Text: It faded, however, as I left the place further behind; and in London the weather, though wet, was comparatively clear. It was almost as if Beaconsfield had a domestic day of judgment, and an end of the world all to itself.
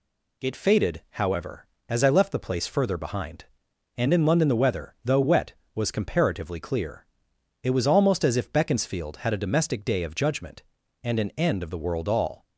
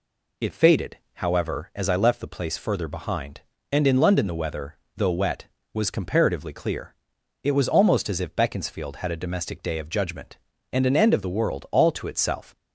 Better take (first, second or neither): second